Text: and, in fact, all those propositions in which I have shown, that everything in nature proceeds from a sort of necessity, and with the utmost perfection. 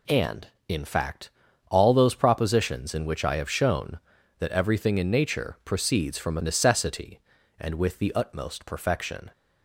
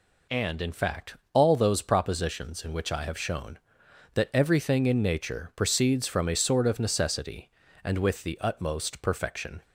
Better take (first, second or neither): second